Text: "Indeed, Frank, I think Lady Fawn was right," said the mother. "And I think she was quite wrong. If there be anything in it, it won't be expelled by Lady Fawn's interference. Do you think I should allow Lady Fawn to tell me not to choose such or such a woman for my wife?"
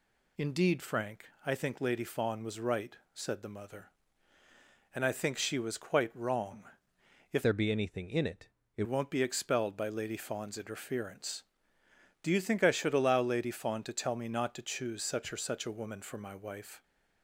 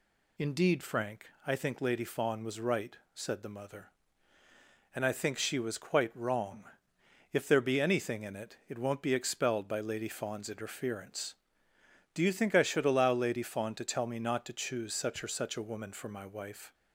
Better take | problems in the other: second | changes voice from "there" to "it"; from 7.4 to 8.8 s; 1.4 s long

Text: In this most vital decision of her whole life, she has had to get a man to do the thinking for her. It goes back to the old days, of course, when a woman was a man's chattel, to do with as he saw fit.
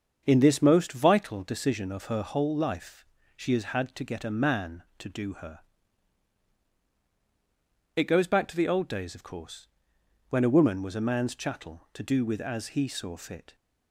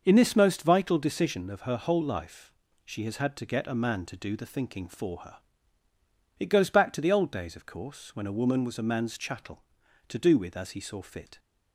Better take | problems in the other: second | starts louder than the rest; until 1.2 s; 7 dB; also in the second // skips "the thinking for"; at 5.3 s

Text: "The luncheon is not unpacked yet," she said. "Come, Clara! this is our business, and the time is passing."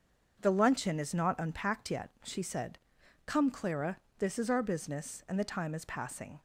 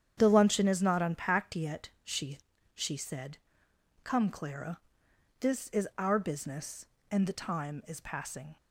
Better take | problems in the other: first | starts louder than the rest; strong; until 1.1 s; 8.5 dB; also in the first // says "she" twice; at 2.7 s

